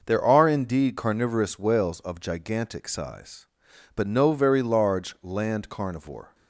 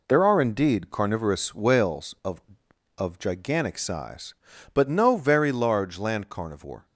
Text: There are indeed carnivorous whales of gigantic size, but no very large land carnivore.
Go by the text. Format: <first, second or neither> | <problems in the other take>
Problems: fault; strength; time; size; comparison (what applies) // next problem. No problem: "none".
first | says "of" twice; at 2.9 s